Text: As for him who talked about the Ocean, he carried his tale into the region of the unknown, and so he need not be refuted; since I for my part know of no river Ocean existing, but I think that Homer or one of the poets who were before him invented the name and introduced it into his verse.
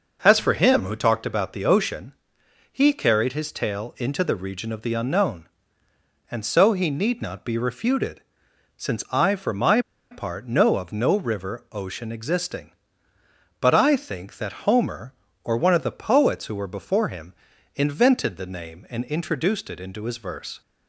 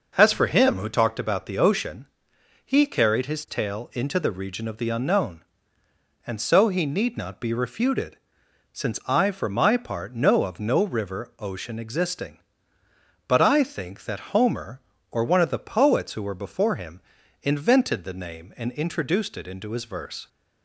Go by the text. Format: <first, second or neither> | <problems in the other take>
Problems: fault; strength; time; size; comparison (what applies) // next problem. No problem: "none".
second | pauses between "my" and "part"; slight; at 9.8 s; 0.30 s long // pauses between "him" and "invented"; at 17.3 s; 0.40 s long; also in the second